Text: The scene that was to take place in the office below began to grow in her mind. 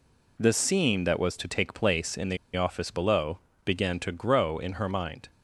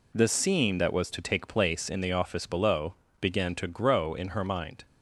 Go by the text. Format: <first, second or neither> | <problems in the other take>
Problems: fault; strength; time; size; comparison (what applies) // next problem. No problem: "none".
second | pauses between "the" and "office"; slight; at 2.3 s; 0.18 s long // pauses between "below" and "began"; slight; at 3.3 s; 0.28 s long; slight in the second